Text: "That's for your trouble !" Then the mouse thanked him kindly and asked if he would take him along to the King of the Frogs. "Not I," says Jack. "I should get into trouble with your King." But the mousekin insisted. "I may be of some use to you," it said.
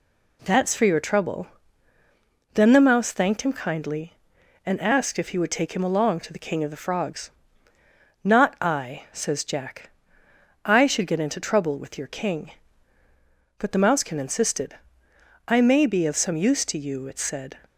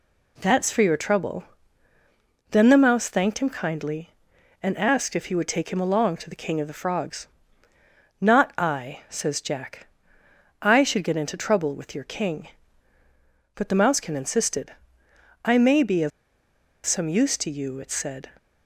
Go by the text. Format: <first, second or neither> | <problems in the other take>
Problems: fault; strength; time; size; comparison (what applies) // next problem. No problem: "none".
first | pauses between "of" and "some"; noticeable; at 16.1 s; 0.76 s long